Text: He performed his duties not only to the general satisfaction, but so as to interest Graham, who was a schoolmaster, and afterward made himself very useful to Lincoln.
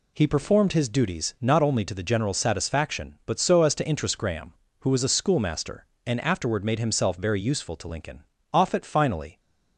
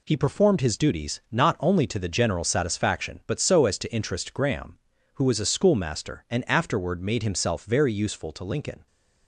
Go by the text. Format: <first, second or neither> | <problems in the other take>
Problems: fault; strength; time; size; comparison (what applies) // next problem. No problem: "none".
second | goes on to say "Offutt finally"; noticeable; from 8.5 s on; 0.88 s long